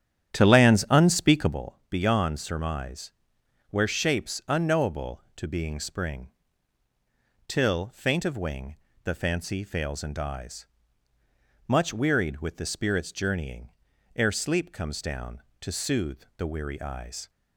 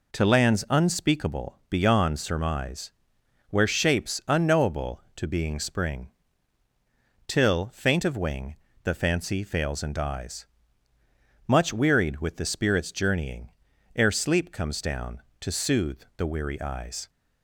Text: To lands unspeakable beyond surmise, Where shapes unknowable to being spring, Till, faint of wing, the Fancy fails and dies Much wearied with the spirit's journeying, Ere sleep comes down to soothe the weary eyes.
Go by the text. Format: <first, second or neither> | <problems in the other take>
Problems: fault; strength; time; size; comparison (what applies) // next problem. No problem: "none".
second | starts louder than the rest; strong; until 1.6 s; 9.5 dB // pauses between "dies" and "Much"; at 10.6 s; 1.0 s long; also in the second // pauses between "soothe" and "the"; slight; at 16.2 s; 0.16 s long; slight in the second